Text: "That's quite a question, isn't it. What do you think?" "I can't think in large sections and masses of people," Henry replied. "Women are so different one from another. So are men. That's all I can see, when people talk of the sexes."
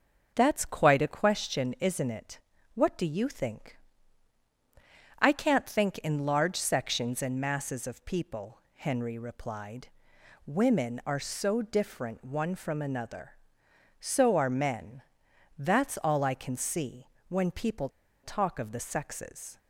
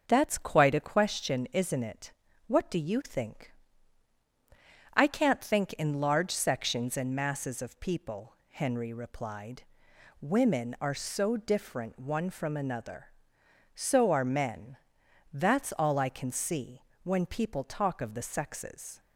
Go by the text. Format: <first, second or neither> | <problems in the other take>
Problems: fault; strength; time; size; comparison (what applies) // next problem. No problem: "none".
second | starts louder than the rest; noticeable; until 1.3 s; 6 dB; noticeable in the second // pauses between "people" and "talk"; slight; at 17.8 s; 0.34 s long